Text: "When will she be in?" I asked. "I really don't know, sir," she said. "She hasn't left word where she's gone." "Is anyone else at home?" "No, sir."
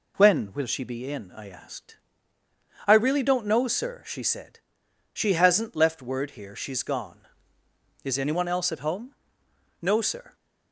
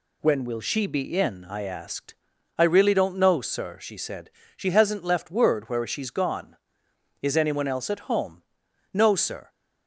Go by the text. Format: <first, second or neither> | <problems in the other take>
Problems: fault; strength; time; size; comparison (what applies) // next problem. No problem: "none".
second | says "here" for "where"; at 6.3 s